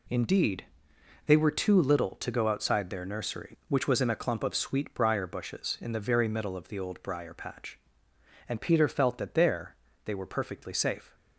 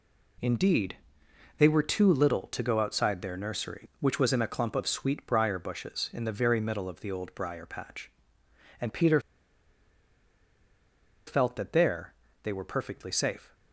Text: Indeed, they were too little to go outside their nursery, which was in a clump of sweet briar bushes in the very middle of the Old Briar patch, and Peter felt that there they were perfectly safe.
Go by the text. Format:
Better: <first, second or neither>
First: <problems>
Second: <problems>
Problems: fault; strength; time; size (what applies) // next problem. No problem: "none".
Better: first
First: pauses between "there" and "they"; slight; at 9.7 s; 0.30 s long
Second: pauses between "Peter" and "felt"; strong; at 9.1 s; 2.0 s long // pauses between "there" and "they"; slight; at 12.1 s; 0.30 s long